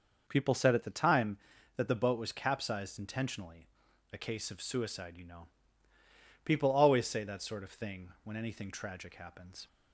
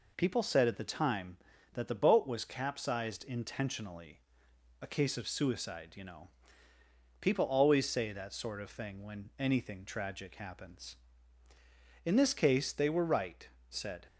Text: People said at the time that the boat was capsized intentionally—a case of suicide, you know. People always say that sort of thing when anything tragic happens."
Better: first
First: none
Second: goes on to say "In this case they were right said"; strong; from 12.0 s on; 2.0 s long

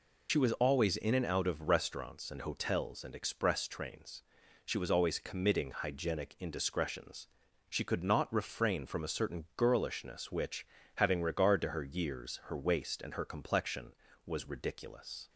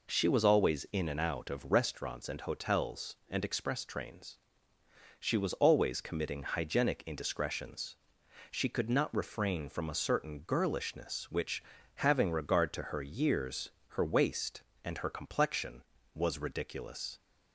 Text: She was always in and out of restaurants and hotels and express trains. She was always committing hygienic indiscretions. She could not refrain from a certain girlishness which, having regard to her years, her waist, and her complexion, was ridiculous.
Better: second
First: loses the start of "She"; at 0.2 s; 45 ms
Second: none

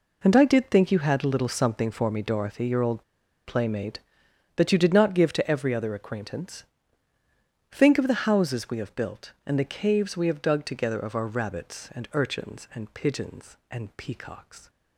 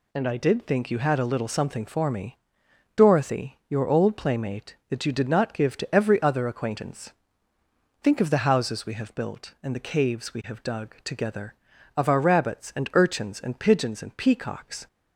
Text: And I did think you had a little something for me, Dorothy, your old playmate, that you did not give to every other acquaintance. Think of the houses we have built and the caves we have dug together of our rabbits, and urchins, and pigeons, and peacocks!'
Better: second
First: pauses between "old" and "playmate"; at 3.0 s; 0.44 s long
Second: none

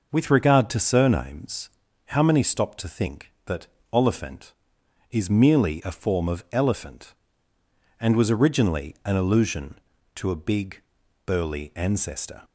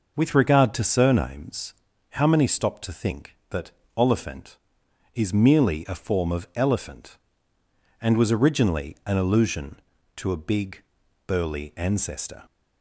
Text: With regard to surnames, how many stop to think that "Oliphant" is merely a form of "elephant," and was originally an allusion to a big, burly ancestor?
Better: neither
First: pauses between "that" and "Oliphant"; slight; at 3.6 s; 0.26 s long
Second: pauses between "that" and "Oliphant"; slight; at 3.7 s; 0.26 s long

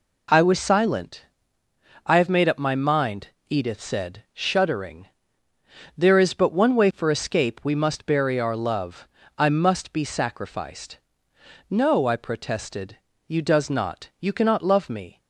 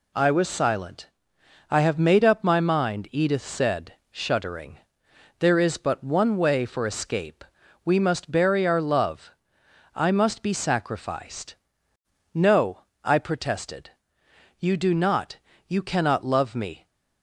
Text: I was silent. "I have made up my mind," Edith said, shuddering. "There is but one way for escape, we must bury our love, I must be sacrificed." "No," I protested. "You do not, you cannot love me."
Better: second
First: says "does" for "do"; at 13.4 s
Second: none

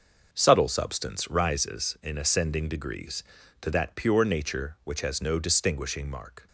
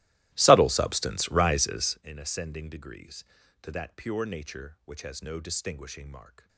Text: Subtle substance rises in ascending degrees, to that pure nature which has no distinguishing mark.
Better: first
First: none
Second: starts louder than the rest; strong; until 2.1 s; 16.5 dB

